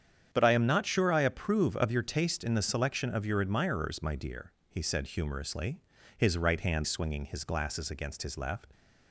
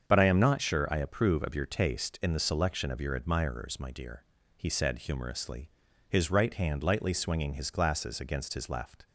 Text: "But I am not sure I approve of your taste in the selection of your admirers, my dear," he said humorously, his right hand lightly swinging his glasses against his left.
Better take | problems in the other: second | starts louder than the rest; strong; until 1.3 s; 8.5 dB; also in the second // skips "lightly"; at 6.8 s

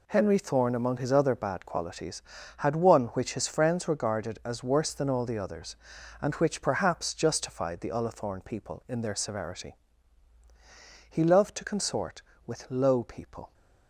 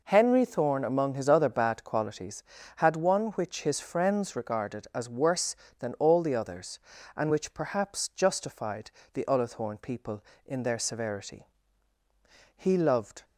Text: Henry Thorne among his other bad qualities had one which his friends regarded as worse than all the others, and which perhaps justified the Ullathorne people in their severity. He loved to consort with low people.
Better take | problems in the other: first | pauses between "justified" and "the"; slight; at 8.9 s; 0.22 s long // stops before "to consort with low people"; at 13.2 s

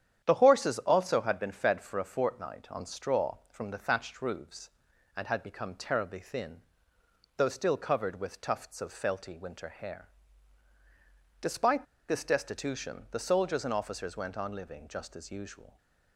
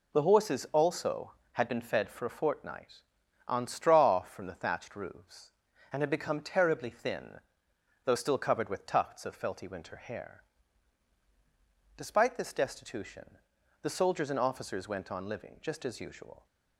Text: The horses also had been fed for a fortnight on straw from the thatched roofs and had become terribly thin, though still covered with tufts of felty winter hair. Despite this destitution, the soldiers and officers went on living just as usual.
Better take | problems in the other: second | starts louder than the rest; strong; until 1.2 s; 9.5 dB // pauses between "Despite" and "this"; slight; at 11.8 s; 0.24 s long

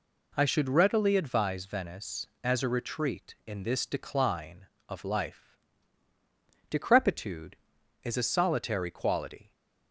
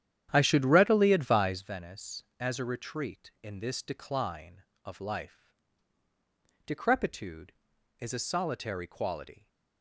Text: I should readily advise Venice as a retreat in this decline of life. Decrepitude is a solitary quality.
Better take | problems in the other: first | starts louder than the rest; strong; until 1.6 s; 10 dB

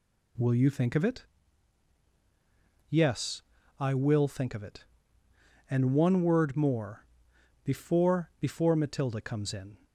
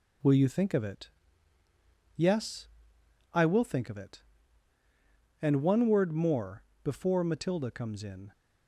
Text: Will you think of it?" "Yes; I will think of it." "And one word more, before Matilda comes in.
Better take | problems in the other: second | says "before" twice; at 8.3 s

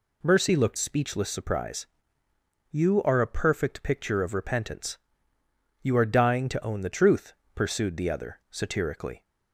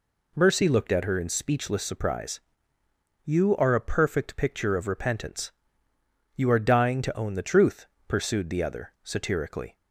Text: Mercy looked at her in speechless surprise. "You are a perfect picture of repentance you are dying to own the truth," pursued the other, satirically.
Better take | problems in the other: second | skips "at her in"; at 0.7 s // pauses between "repentance" and "you"; noticeable; at 4.9 s; 0.84 s long; noticeable in the second

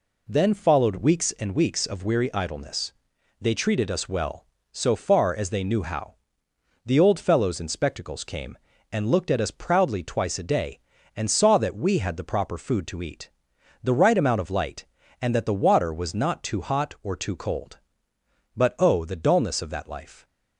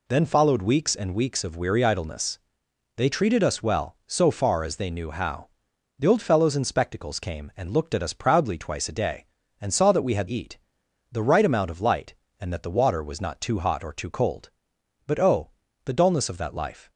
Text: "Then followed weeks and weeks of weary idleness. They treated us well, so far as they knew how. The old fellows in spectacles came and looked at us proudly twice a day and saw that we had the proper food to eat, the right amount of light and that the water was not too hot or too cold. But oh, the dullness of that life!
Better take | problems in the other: first | skips "the proper food to"; at 10.2 s

